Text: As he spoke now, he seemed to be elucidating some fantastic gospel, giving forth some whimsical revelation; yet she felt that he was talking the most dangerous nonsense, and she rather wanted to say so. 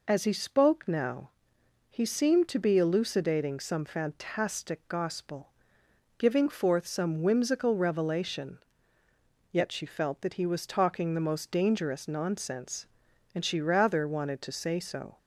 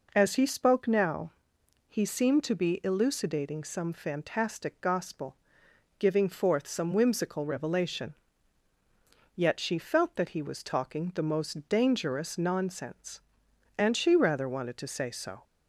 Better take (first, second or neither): neither